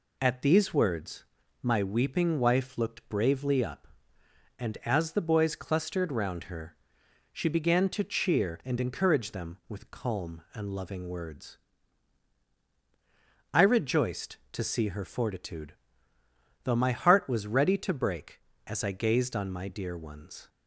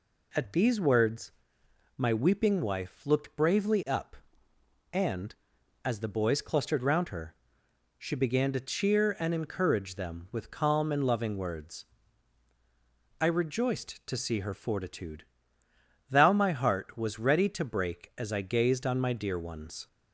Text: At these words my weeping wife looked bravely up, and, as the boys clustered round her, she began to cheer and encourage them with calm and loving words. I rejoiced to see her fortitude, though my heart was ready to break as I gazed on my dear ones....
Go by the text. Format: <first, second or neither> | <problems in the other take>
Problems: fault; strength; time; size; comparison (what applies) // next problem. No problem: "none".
first | pauses between "words" and "my"; noticeable; at 1.3 s; 0.66 s long; also in the first // says "thou" for "though"; at 16.0 s